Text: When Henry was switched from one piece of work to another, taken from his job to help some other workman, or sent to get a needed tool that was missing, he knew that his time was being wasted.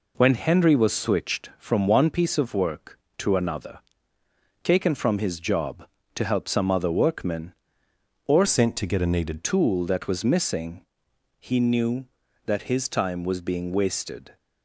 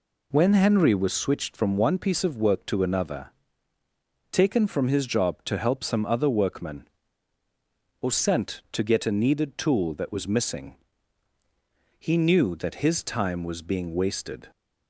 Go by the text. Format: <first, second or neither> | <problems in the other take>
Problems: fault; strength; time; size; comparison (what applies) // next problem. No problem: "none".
second | changes voice from "sent" to "needed"; from 8.4 to 9.4 s; 1.0 s long